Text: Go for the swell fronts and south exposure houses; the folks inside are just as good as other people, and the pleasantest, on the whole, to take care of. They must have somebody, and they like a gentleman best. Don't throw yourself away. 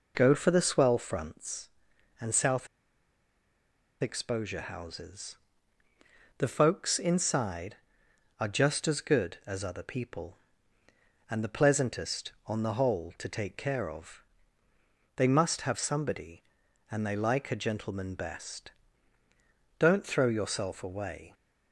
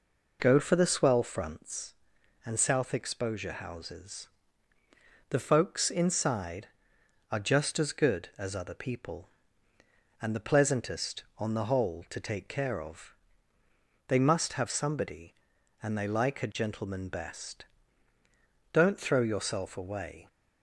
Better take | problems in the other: second | pauses between "south" and "exposure"; strong; at 2.6 s; 1.3 s long

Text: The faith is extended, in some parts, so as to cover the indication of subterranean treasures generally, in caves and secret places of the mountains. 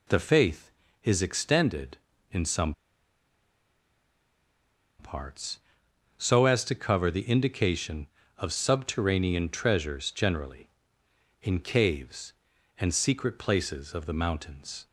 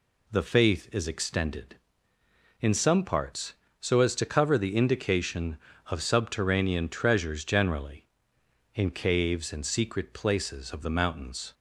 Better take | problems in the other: second | pauses between "some" and "parts"; strong; at 2.7 s; 2.2 s long

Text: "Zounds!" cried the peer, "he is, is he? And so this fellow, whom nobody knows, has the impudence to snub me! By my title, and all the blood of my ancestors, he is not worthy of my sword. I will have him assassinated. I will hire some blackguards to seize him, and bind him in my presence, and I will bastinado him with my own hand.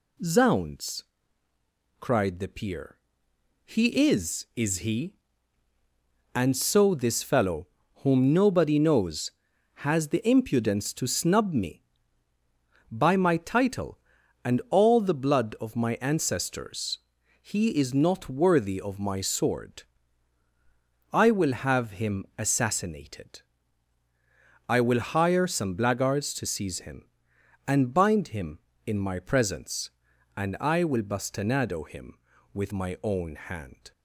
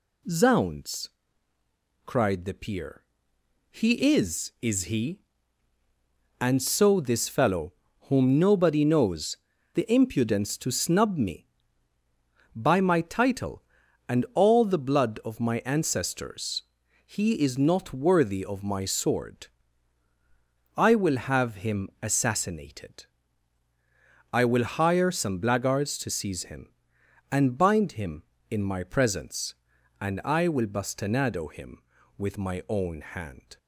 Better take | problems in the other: first | skips "has"; at 9.5 s

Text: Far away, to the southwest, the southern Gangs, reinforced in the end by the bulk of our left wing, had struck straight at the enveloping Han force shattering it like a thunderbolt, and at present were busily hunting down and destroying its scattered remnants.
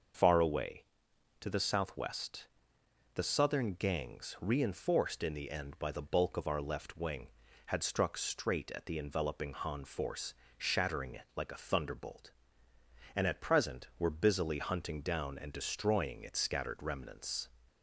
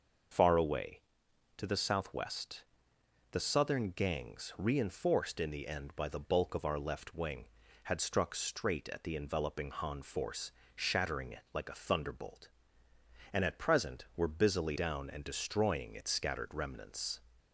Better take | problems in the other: first | starts louder than the rest; until 1.9 s; 6 dB; also in the first // pauses between "force" and "shattering"; slight; at 10.5 s; 0.24 s long; slight in the first // skips "hunting"; at 14.7 s

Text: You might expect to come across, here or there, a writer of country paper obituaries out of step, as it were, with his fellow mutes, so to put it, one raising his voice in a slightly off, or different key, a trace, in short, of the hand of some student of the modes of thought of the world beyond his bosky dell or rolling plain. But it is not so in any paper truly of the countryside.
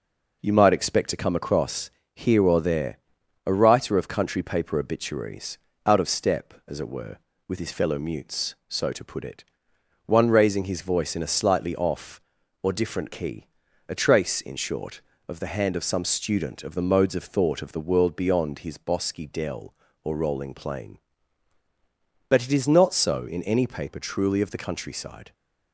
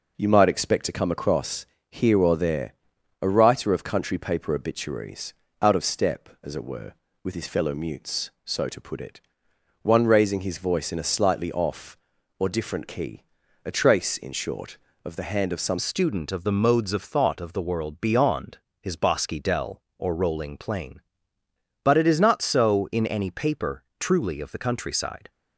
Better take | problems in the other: first | pauses between "obituaries" and "out"; slight; at 5.3 s; 0.28 s long; slight in the first // changes voice at "student"; from 15.7 s on; 9.6 s long // pauses between "beyond" and "his"; slight; at 18.5 s; 0.22 s long // pauses between "paper" and "truly"; slight; at 23.8 s; 0.16 s long

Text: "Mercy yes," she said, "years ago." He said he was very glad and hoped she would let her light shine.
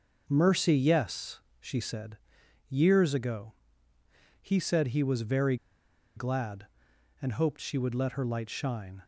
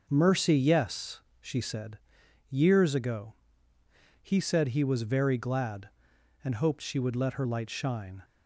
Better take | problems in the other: second | starts louder than the rest; until 1.2 s; 6 dB; also in the second // pauses between "very" and "glad"; noticeable; at 5.5 s; 0.59 s long

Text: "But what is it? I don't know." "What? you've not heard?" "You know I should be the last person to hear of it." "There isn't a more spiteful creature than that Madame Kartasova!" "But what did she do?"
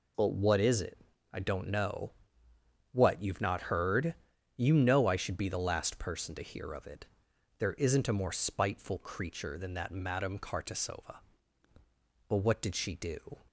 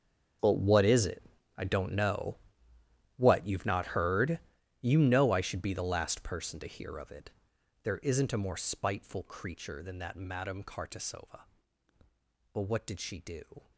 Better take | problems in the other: first | gets quieter; strong; throughout; 17 dB

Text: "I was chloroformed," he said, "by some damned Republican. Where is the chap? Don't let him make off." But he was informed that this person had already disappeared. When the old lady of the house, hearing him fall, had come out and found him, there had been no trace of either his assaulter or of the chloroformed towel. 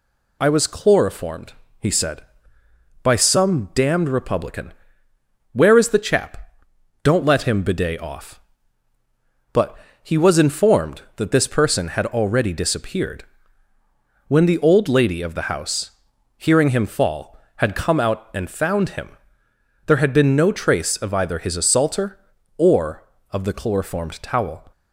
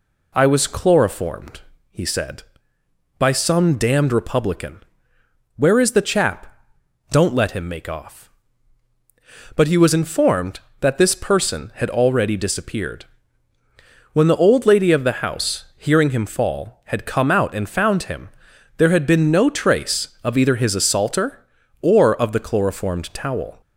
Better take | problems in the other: second | says "bidet" for "make"; at 7.6 s // pauses between "But" and "he"; slight; at 9.7 s; 0.26 s long

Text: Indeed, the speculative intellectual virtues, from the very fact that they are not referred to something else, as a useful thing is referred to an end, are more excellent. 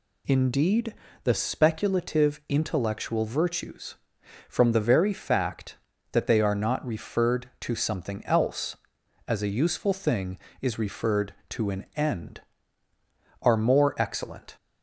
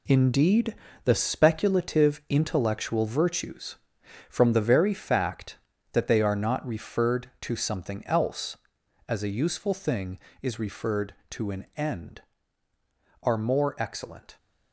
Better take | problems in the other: first | gets quieter; strong; throughout; 8.5 dB

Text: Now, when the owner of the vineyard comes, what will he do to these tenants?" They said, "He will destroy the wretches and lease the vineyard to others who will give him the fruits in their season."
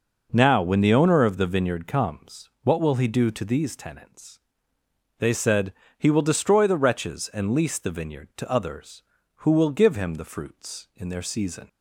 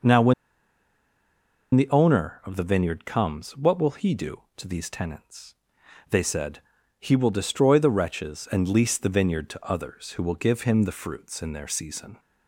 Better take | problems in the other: first | pauses between "when" and "the"; strong; at 0.3 s; 1.4 s long

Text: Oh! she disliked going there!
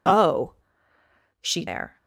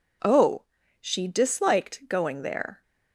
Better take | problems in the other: second | skips "disliked going"; at 1.6 s

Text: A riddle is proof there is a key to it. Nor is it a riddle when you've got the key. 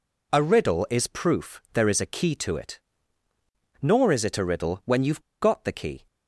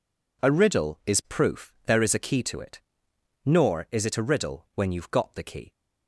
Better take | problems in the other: second | pauses between "you've" and "got"; slight; at 5.2 s; 0.19 s long

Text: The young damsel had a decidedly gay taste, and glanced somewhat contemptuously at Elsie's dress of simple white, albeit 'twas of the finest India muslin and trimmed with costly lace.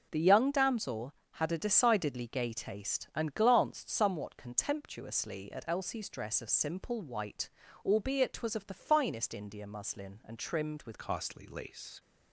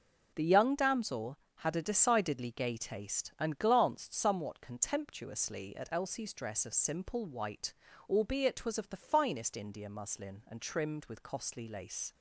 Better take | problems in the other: second | changes voice at "costly"; from 10.9 s on; 1.0 s long

